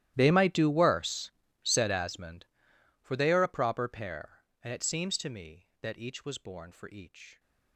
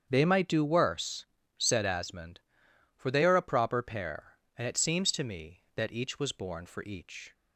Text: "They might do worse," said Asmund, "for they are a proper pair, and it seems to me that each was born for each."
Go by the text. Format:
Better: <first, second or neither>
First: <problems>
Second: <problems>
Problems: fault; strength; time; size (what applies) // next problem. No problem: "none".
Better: second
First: gets quieter; strong; throughout; 23 dB // starts louder than the rest; strong; until 1.1 s; 13 dB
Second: starts louder than the rest; strong; until 1.1 s; 7.5 dB